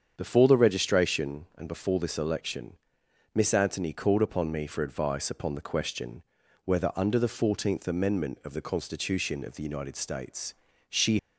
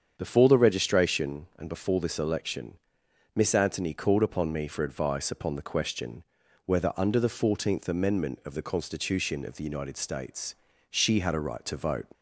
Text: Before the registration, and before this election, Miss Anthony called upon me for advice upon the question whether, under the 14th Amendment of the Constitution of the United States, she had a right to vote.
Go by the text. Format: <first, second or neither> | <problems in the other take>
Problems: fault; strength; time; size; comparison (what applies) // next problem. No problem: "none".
second | starts louder than the rest; strong; until 1.1 s; 7.5 dB; strong in the second // pauses between "question" and "whether"; at 6.2 s; 0.42 s long; also in the second // stops before "had a right to vote"; at 11.1 s